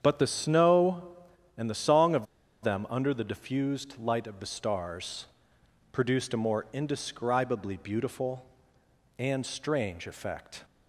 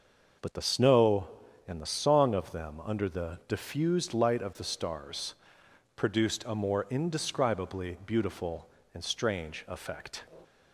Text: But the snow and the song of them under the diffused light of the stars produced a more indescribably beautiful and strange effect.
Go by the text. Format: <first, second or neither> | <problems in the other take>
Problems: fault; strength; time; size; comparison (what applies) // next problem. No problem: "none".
second | starts louder than the rest; strong; until 1.0 s; 8 dB; also in the second // pauses between "of" and "them"; at 2.2 s; 0.37 s long // pauses between "stars" and "produced"; noticeable; at 5.2 s; 0.66 s long; noticeable in the second